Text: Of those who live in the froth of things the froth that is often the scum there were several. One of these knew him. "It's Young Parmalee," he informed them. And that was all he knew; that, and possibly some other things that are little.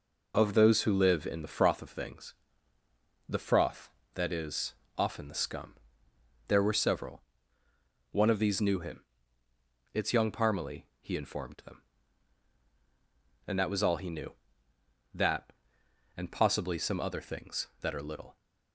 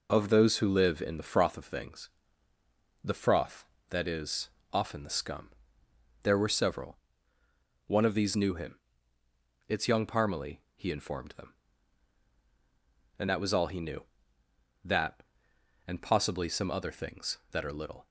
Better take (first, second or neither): neither